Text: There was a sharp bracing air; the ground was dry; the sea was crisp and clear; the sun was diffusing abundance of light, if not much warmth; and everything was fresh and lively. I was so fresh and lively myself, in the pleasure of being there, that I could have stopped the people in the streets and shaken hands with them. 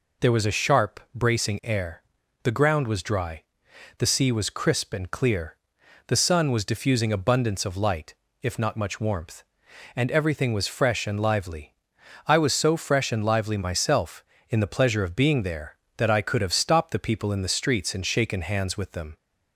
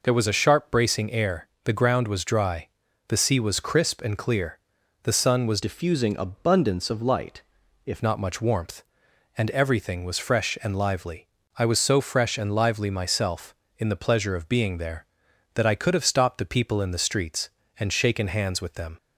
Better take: first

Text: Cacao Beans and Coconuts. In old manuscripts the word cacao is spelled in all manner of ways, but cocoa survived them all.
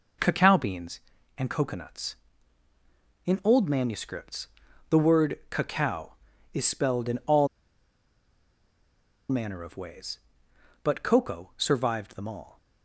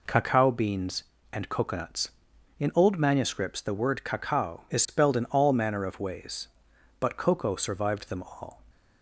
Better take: second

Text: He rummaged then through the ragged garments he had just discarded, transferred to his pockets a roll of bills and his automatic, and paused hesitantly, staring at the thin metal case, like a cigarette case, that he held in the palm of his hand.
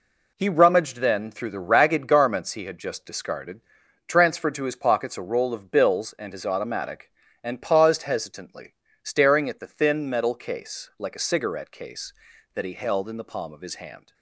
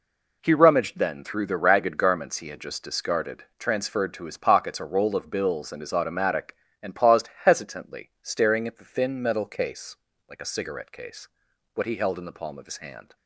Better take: first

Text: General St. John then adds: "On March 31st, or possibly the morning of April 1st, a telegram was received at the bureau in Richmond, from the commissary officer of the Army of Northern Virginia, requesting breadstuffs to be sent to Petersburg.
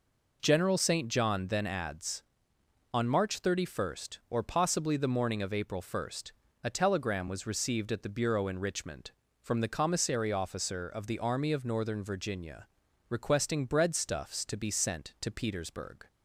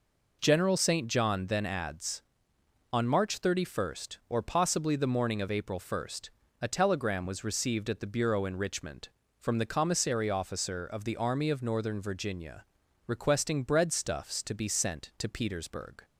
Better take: neither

